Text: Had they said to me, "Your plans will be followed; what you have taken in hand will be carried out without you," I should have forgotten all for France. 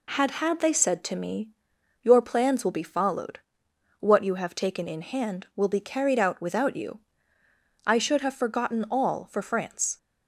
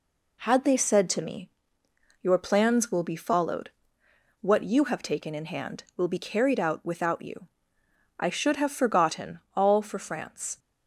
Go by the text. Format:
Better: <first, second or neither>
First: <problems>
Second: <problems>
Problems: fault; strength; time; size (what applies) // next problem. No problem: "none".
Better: second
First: says "Had" twice; at 0.3 s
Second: none